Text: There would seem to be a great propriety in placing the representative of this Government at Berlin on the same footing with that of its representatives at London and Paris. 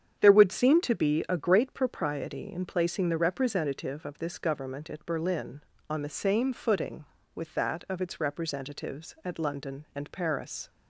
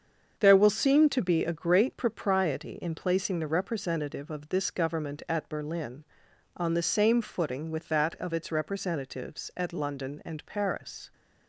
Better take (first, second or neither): first